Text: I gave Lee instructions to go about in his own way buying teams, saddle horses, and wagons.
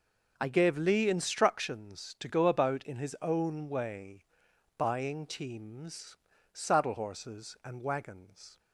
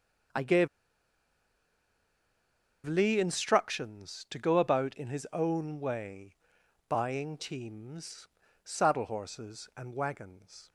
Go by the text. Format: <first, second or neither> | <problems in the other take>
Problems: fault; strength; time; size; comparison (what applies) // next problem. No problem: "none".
first | pauses between "gave" and "Lee"; strong; at 0.6 s; 2.1 s long // pauses between "way" and "buying"; noticeable; at 6.3 s; 0.52 s long; noticeable in the first